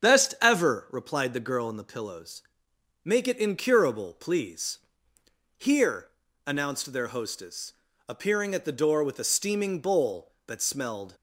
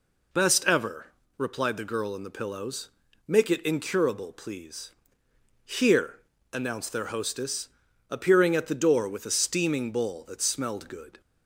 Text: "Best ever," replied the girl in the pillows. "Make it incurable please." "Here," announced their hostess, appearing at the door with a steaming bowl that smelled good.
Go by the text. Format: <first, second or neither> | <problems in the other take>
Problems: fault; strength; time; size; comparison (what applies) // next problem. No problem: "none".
second | starts louder than the rest; strong; until 1.1 s; 7.5 dB // stops before "good"; at 11.1 s